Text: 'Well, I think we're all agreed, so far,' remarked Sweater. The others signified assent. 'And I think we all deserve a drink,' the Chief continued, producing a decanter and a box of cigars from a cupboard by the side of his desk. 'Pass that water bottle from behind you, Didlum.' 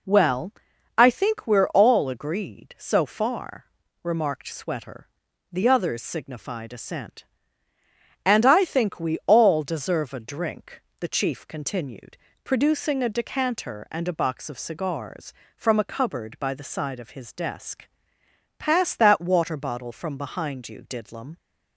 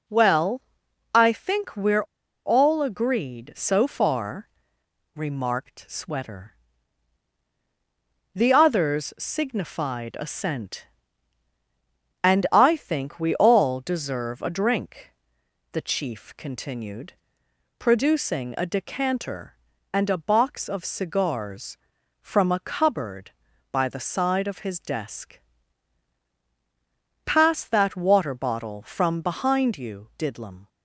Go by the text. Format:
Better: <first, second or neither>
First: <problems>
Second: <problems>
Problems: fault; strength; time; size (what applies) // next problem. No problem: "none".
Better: first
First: none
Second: pauses between "we're" and "all"; at 2.0 s; 0.41 s long